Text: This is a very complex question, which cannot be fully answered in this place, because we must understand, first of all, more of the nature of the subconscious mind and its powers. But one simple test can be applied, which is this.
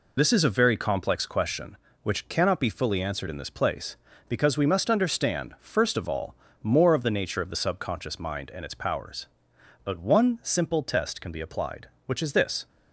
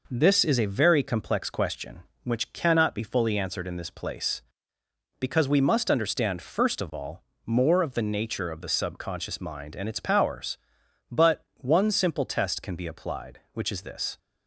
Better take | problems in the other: second | loses the start of "This"; at 0.1 s; 45 ms

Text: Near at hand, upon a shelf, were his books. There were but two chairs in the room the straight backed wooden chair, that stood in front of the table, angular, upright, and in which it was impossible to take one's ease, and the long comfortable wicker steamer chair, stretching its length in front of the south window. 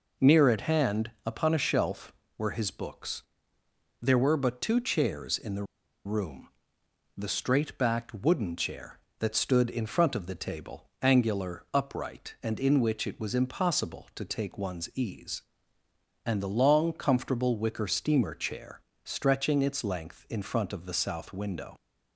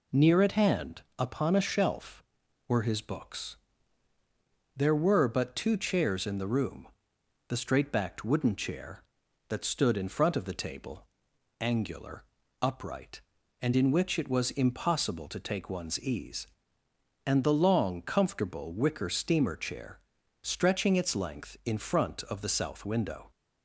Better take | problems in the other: second | pauses between "the" and "room"; at 5.6 s; 0.41 s long // pauses between "room" and "the"; noticeable; at 6.4 s; 0.70 s long; noticeable in the second

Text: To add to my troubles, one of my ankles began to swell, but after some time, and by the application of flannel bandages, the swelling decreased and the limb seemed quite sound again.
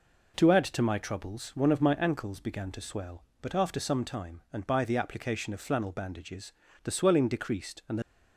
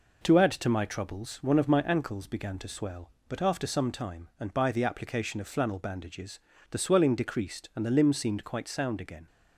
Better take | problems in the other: second | stops before "limb seemed quite sound again"; at 8.0 s

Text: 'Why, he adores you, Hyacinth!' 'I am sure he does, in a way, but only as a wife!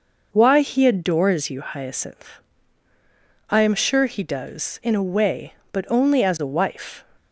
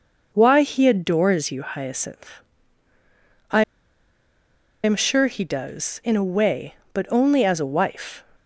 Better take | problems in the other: first | pauses between "I" and "am"; at 3.6 s; 1.2 s long

